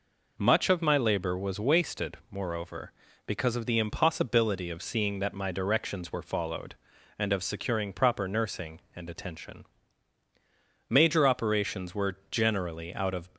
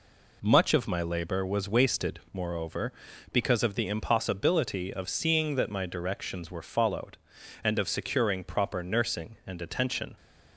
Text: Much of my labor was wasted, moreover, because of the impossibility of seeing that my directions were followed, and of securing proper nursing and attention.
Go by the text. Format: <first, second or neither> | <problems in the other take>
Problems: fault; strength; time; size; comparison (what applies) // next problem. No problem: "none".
second | goes on to say "Major operations were generally out of"; strong; from 10.8 s on; 2.4 s long